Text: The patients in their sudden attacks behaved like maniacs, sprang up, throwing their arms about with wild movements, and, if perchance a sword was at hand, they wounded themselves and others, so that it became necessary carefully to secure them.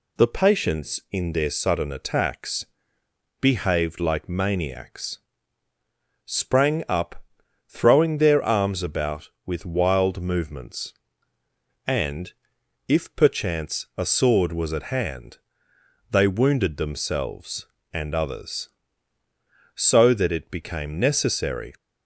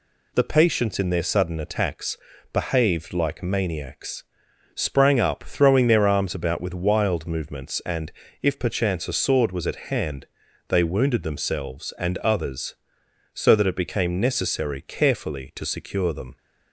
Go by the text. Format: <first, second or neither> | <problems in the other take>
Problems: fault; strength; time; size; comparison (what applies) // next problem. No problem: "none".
second | pauses between "attacks" and "behaved"; noticeable; at 2.6 s; 0.78 s long; slight in the second // stops before "carefully to secure them"; at 21.7 s